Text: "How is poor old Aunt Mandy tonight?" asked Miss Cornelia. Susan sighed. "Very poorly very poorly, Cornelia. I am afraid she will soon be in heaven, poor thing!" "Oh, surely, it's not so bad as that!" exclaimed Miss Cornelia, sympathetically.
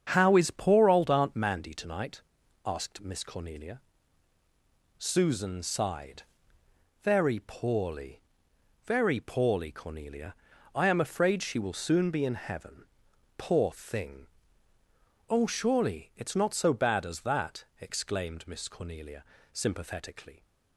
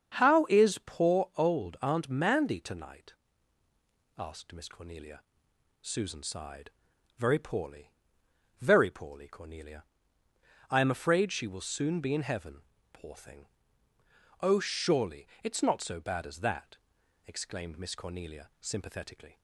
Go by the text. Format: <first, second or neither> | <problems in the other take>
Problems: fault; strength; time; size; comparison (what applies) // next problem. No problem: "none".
neither | starts louder than the rest; strong; the same in both // pauses between "poorly" and "very"; noticeable; the same in both